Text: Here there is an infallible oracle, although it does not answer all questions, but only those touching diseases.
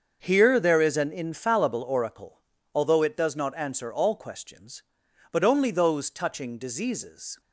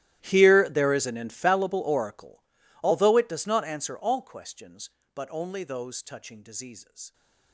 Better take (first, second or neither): first